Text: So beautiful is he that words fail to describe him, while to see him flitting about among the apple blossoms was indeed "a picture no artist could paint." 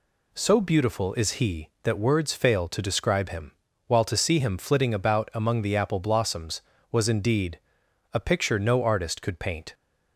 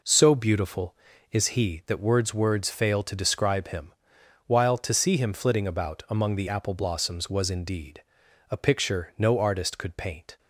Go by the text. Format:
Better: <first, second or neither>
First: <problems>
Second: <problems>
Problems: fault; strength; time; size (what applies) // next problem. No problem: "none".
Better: first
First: pauses between "indeed" and "a"; noticeable; at 7.5 s; 0.56 s long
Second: says "words" twice; at 2.3 s // pauses between "indeed" and "a"; noticeable; at 8.0 s; 0.46 s long